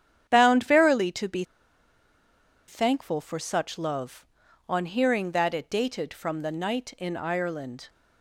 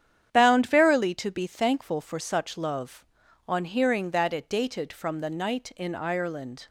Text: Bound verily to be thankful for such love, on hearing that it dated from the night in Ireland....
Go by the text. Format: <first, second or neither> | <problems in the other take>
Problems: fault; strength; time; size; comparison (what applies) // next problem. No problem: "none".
second | starts louder than the rest; strong; until 1.3 s; 9 dB; strong in the second // pauses between "be" and "thankful"; at 1.4 s; 1.2 s long